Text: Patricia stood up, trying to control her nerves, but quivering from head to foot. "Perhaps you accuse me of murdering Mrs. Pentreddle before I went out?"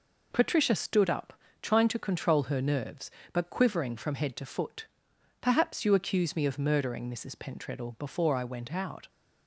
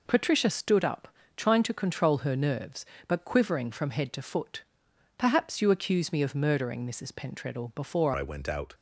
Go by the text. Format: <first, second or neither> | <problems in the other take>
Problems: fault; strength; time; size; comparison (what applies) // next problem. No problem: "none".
first | changes voice at "I"; from 8.1 s on; 0.6 s long